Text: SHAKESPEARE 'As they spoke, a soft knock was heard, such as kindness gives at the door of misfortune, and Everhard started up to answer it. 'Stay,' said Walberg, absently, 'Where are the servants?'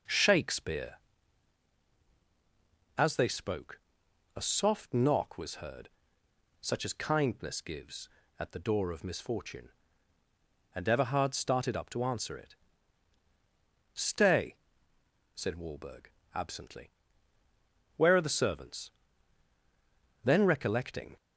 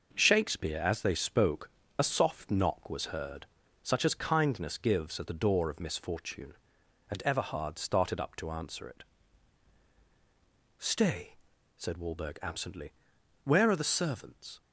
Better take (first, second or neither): second